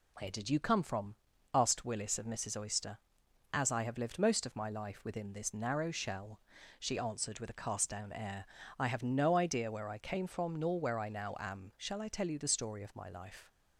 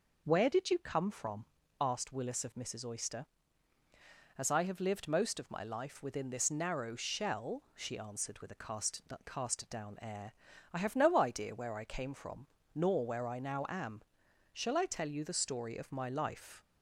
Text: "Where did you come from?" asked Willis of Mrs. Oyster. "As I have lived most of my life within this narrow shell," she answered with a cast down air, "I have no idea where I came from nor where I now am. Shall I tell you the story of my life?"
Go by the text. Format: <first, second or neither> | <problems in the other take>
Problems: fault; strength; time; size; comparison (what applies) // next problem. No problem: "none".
first | says "cast" twice; at 9.2 s // pauses between "from" and "nor"; slight; at 12.4 s; 0.26 s long